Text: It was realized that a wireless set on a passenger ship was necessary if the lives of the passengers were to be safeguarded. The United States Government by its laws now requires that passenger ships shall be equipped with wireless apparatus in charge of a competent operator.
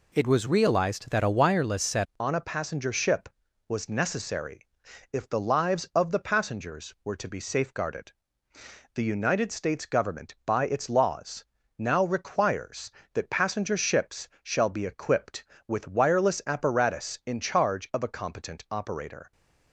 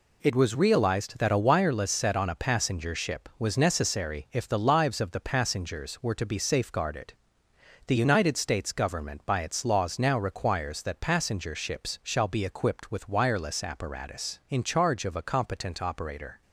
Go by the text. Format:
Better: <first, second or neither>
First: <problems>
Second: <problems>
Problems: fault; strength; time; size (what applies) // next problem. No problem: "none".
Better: second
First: changes voice at "on"; from 2.1 s on; 17.2 s long // pauses between "necessary" and "if"; at 4.6 s; 0.44 s long // pauses between "laws" and "now"; slight; at 11.4 s; 0.34 s long // pauses between "ships" and "shall"; slight; at 14.2 s; 0.16 s long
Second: none